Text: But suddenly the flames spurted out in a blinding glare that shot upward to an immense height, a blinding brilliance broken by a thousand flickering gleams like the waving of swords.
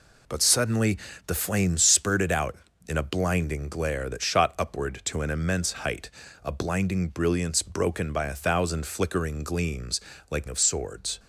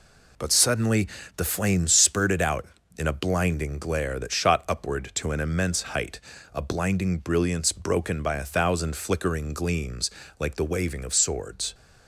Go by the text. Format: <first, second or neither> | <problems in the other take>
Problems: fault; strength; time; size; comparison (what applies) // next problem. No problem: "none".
second | pauses between "suddenly" and "the"; slight; at 0.9 s; 0.30 s long; slight in the second // pauses between "gleams" and "like"; slight; at 9.9 s; 0.30 s long; slight in the second // skips "the waving"; at 10.4 s